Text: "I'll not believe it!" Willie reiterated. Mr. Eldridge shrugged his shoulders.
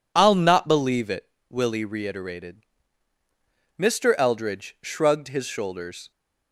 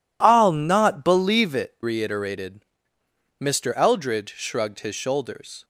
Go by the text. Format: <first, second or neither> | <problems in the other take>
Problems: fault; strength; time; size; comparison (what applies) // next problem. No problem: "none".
first | skips "Willie"; at 1.7 s